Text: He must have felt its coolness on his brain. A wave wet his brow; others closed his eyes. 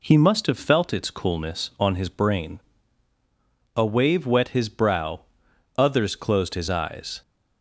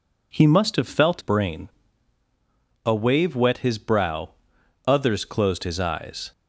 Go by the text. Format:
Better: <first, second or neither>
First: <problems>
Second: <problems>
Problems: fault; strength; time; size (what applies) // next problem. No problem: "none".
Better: first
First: none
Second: skips "its coolness on his"; at 1.2 s